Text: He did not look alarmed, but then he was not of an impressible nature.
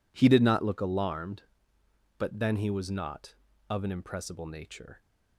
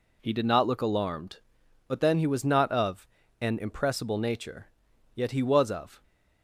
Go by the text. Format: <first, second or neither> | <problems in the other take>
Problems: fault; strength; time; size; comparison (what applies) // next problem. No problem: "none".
first | pauses between "of" and "an"; slight; at 3.0 s; 0.34 s long // goes on to say "Yet he was of"; noticeable; from 5.1 s on; 0.88 s long